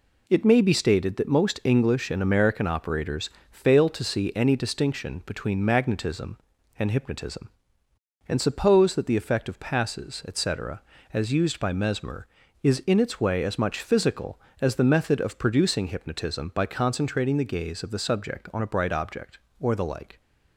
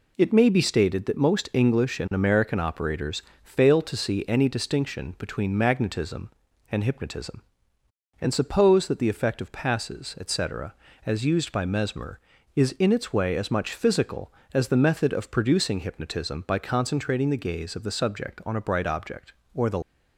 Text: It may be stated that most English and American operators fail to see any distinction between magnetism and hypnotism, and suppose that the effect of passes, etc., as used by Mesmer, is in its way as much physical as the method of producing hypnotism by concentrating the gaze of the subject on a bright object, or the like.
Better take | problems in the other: first | pauses between "operators" and "fail"; slight; at 3.2 s; 0.22 s long; slight in the first // stops before "like"; at 19.8 s

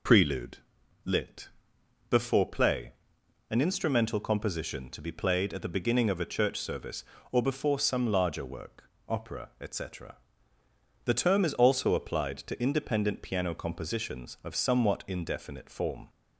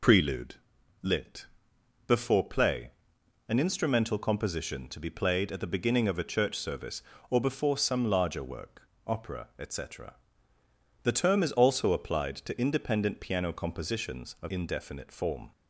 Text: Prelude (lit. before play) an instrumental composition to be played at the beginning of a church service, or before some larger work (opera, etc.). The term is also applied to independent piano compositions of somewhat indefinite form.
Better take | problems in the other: first | skips "somewhat"; at 14.4 s

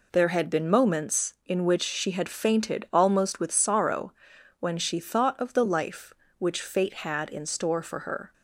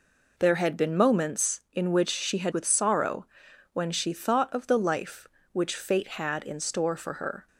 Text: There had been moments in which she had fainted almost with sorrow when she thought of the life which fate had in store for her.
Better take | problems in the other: first | skips "fainted almost"; at 2.5 s // pauses between "sorrow" and "when"; noticeable; at 3.2 s; 0.48 s long; noticeable in the first

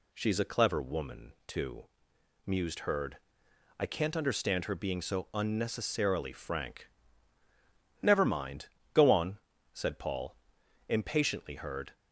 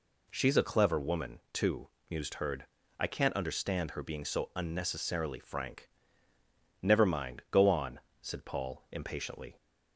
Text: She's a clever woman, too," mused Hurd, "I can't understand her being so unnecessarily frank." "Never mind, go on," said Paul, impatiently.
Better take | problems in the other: second | goes on to say "Hurd"; slight; from 11.5 s on; 0.40 s long

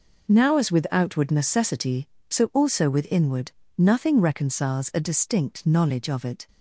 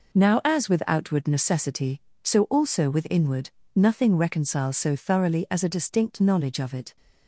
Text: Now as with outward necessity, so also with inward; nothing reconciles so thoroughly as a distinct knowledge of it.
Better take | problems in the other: second | skips "so thoroughly as"; at 4.9 s

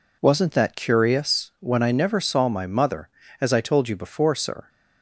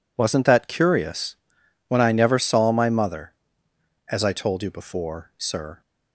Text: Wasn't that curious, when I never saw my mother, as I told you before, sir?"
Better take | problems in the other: neither | none

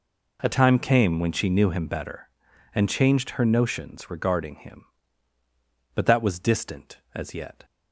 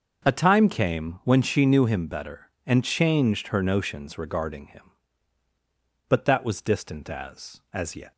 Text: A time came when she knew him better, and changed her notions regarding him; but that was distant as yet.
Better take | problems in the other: first | starts louder than the rest; until 1.3 s; 6.5 dB // says "as" twice; at 7.7 s

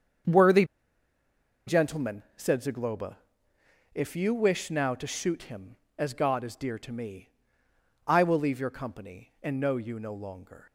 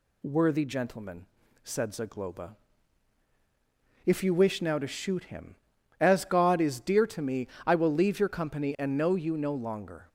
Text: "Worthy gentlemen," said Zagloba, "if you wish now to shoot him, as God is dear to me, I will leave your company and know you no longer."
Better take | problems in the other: second | starts louder than the rest; strong; until 2.4 s; 7 dB // pauses between "Worthy" and "gentlemen"; at 0.6 s; 1.0 s long

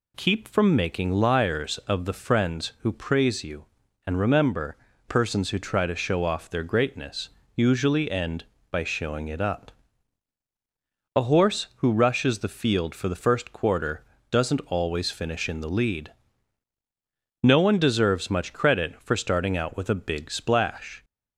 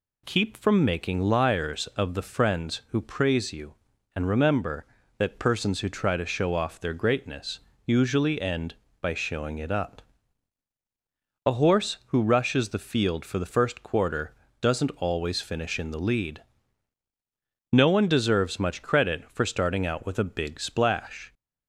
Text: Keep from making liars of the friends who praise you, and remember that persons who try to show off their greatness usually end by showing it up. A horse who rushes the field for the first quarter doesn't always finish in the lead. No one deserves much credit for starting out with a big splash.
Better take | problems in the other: second | skips "that"; at 4.9 s // pauses between "greatness" and "usually"; slight; at 7.2 s; 0.26 s long; slight in the second // pauses between "quarter" and "doesn't"; slight; at 14.0 s; 0.28 s long; slight in the second

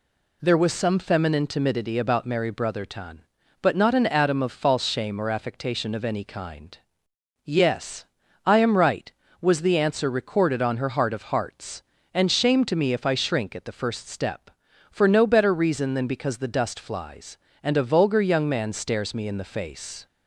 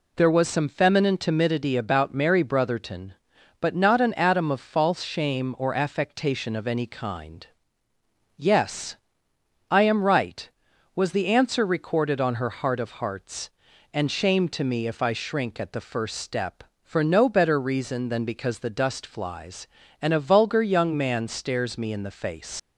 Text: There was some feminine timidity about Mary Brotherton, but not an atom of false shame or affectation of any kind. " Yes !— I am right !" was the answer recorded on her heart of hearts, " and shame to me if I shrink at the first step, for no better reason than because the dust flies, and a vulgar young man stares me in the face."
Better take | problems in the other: first | leaves "face" unfinished; at 22.5 s; 70 ms

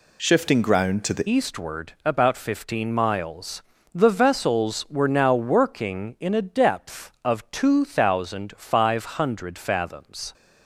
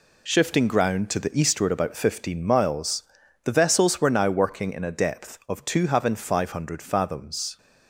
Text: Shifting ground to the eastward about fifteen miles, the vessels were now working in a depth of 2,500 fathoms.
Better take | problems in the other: second | changes voice at "eastward"; from 1.2 s on; 9.1 s long

